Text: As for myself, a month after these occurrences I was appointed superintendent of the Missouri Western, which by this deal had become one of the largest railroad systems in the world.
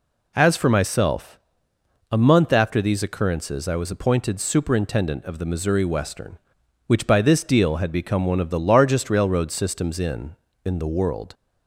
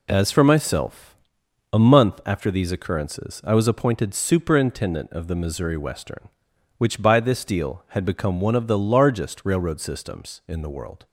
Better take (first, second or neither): second